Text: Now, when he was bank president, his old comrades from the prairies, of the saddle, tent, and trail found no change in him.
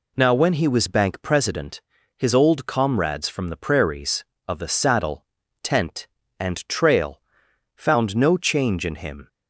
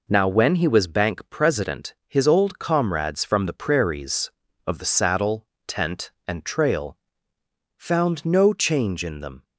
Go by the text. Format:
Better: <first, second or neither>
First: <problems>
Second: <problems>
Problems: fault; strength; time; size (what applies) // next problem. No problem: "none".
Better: first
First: pauses between "trail" and "found"; noticeable; at 7.1 s; 0.54 s long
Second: pauses between "trail" and "found"; noticeable; at 6.9 s; 0.80 s long // says "them" for "him"; at 9.1 s